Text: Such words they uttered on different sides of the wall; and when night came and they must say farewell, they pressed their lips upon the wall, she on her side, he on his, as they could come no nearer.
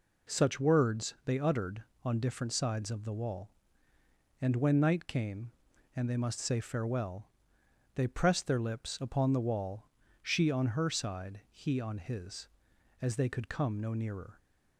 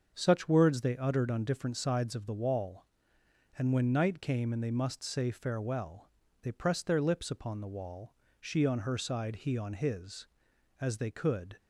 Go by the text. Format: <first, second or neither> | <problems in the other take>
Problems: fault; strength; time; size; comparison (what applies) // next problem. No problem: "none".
first | starts louder than the rest; until 1.1 s; 6.5 dB // stops before "come no nearer"; at 11.5 s